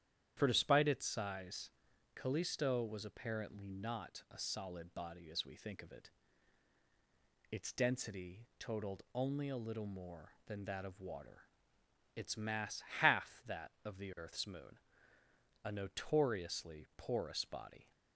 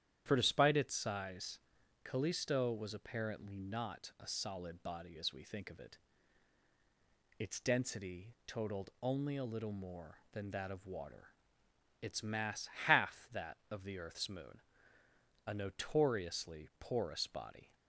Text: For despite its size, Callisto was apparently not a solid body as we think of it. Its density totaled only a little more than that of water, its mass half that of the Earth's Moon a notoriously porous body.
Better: neither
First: starts louder than the rest; strong; until 1.3 s; 10 dB // pauses between "mass" and "half"; slight; at 12.8 s; 0.16 s long // pauses between "Moon" and "a"; noticeable; at 14.7 s; 0.84 s long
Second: starts louder than the rest; strong; until 1.2 s; 10 dB // pauses between "mass" and "half"; slight; at 12.6 s; 0.16 s long // pauses between "Moon" and "a"; noticeable; at 14.6 s; 0.84 s long

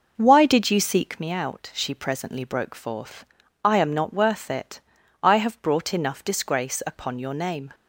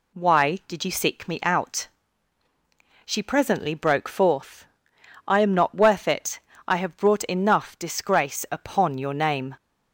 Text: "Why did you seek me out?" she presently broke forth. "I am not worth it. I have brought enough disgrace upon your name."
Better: second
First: starts louder than the rest; noticeable; until 1.2 s; 5.5 dB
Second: none

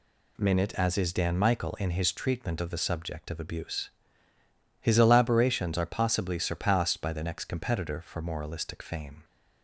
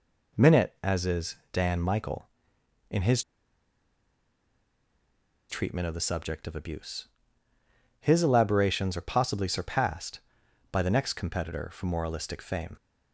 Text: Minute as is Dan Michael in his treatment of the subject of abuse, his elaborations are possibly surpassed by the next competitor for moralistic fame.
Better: first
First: none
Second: pauses between "is" and "Dan"; slight; at 1.3 s; 0.18 s long // pauses between "his" and "treatment"; strong; at 3.2 s; 2.2 s long

